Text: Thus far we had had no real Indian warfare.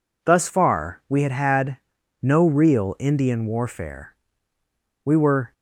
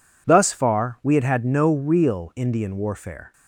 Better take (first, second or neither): second